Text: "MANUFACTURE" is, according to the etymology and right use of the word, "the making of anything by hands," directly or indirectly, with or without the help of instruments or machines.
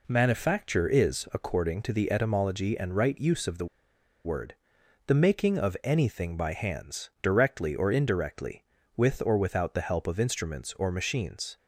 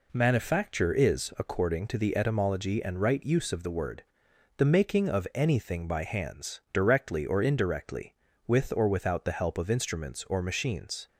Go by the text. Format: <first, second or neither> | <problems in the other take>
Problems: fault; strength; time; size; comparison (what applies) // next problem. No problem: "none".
second | pauses between "the" and "word"; noticeable; at 3.6 s; 0.59 s long